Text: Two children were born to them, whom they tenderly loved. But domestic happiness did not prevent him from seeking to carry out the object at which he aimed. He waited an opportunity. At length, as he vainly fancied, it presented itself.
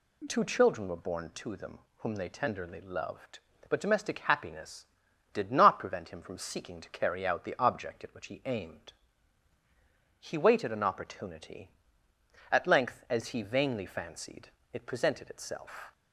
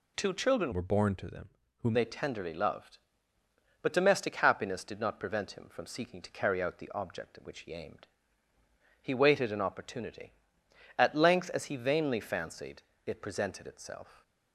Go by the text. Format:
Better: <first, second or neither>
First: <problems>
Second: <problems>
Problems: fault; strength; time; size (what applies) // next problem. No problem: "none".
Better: first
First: none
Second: changes voice from "were" to "whom"; from 0.7 to 1.9 s; 1.2 s long